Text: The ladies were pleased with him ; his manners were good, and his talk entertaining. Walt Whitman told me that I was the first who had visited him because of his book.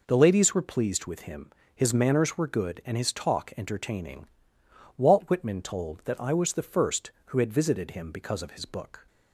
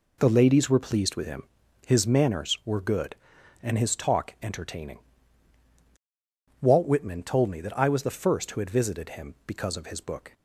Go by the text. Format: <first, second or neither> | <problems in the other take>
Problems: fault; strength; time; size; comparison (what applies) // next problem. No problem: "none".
second | skips "me"; at 6.0 s